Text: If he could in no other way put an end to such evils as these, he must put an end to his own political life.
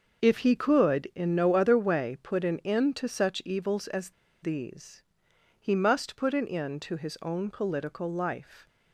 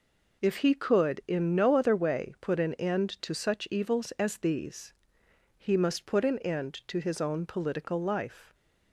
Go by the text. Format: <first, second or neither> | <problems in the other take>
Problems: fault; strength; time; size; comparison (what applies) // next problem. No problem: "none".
second | starts louder than the rest; noticeable; until 1.2 s; 6 dB // pauses between "as" and "these"; slight; at 4.1 s; 0.30 s long